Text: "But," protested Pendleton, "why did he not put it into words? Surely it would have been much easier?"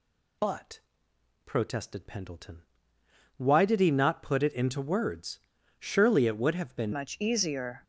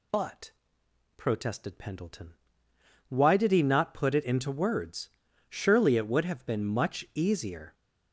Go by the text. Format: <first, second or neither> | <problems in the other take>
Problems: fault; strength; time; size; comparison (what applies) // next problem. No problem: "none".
second | changes voice at "much"; from 6.9 s on; 0.9 s long